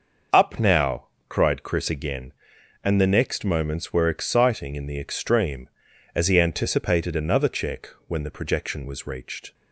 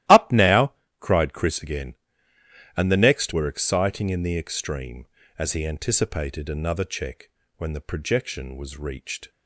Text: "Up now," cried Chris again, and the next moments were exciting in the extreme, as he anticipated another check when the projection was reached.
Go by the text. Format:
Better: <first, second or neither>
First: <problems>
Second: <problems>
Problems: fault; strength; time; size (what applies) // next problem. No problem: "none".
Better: first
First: starts louder than the rest; noticeable; until 1.5 s; 6 dB // pauses between "check" and "when"; slight; at 7.8 s; 0.18 s long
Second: starts louder than the rest; strong; until 1.3 s; 15 dB // skips "moments"; at 3.3 s // pauses between "check" and "when"; slight; at 7.3 s; 0.26 s long